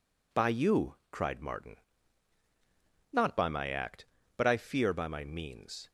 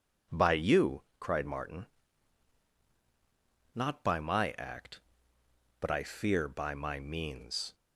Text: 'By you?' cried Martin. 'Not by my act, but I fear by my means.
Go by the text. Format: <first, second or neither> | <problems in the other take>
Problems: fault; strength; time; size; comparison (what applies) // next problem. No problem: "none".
neither | none